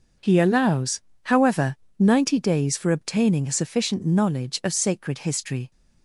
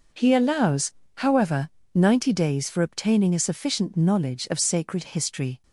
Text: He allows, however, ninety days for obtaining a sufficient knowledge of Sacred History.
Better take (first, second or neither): neither